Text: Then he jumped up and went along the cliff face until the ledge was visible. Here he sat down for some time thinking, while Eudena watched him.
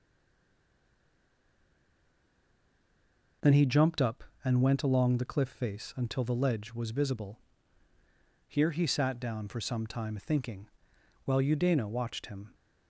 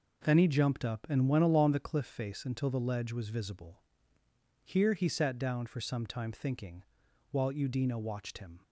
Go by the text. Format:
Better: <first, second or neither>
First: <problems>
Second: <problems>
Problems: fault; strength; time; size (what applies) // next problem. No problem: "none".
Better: second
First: stays silent before the first word; strong; until 3.4 s; 3.4 s long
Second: none